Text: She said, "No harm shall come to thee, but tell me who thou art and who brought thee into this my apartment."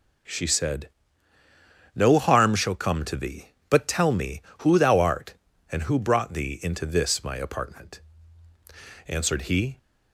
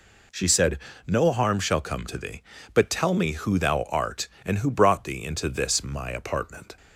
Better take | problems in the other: second | goes on to say "Answered he"; noticeable; from 9.0 s on; 0.72 s long

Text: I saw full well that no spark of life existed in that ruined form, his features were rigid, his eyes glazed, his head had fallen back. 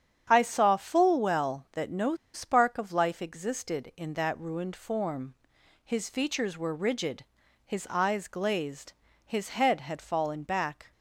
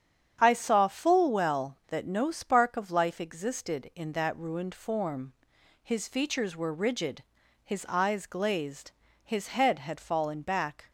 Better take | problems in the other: second | starts louder than the rest; strong; until 1.3 s; 8.5 dB; strong in the second // pauses between "no" and "spark"; slight; at 2.1 s; 0.19 s long

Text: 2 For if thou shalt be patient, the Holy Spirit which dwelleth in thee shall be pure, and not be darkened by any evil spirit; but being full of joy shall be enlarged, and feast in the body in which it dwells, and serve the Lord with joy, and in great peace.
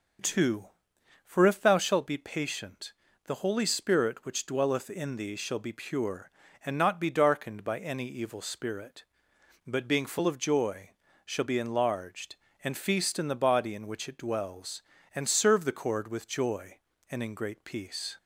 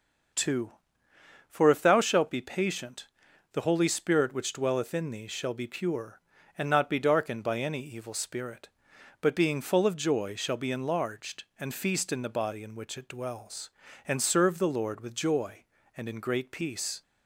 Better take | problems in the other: second | pauses between "joy" and "shall"; slight; at 10.9 s; 0.34 s long // says "Cord" for "Lord"; at 15.7 s

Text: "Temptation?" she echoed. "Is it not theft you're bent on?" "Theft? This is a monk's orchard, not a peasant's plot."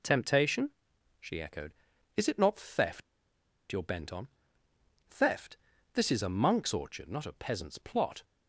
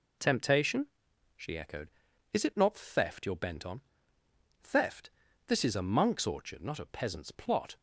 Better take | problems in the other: second | pauses between "theft" and "you're"; noticeable; at 3.0 s; 0.67 s long

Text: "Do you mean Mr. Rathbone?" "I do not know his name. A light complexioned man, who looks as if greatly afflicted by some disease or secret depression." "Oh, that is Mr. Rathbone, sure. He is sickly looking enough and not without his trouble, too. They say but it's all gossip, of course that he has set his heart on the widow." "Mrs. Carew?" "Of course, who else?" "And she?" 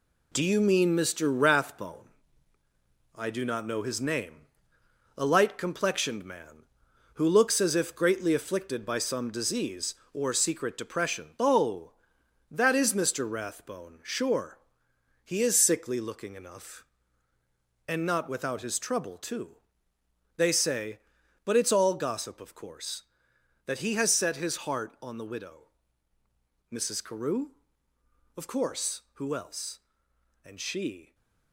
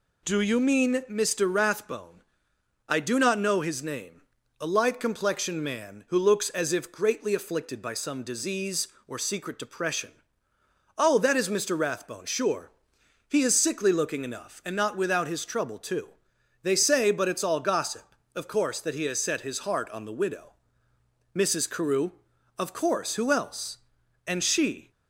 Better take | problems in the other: second | gets quieter; throughout; 6.5 dB

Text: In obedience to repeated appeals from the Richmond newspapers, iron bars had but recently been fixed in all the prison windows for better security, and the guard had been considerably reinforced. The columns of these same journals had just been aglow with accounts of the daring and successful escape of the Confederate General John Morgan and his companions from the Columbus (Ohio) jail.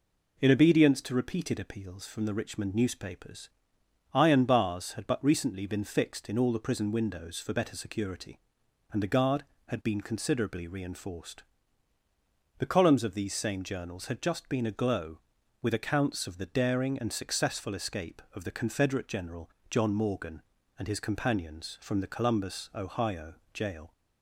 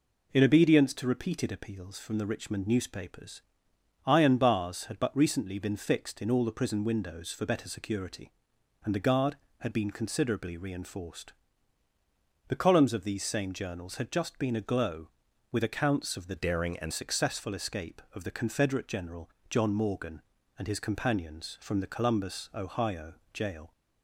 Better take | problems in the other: first | changes voice from "daring" to "and"; from 16.3 to 16.9 s; 0.6 s long // pauses between "General" and "John"; slight; at 19.2 s; 0.18 s long; slight in the first

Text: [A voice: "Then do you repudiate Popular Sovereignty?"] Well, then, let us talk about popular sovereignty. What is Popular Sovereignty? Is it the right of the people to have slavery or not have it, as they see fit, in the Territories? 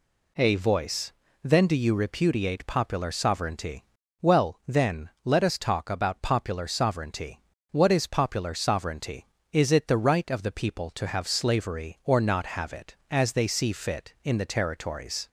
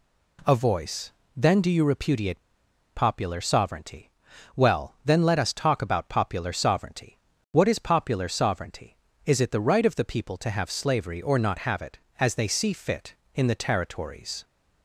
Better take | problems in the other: first | pauses between "repudiate" and "Popular"; noticeable; at 2.3 s; 0.55 s long

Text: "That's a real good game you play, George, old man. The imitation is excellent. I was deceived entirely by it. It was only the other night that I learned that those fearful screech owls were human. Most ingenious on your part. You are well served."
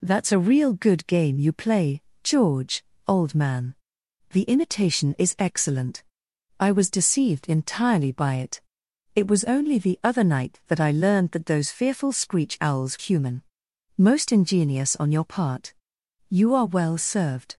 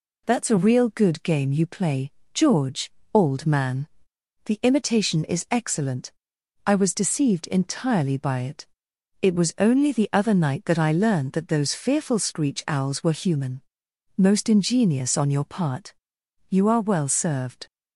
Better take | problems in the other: second | skips "were"; at 12.9 s

